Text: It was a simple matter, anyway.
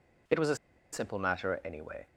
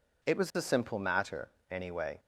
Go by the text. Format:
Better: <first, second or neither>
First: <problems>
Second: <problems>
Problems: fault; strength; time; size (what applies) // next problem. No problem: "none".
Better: second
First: pauses between "a" and "simple"; at 0.5 s; 0.37 s long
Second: none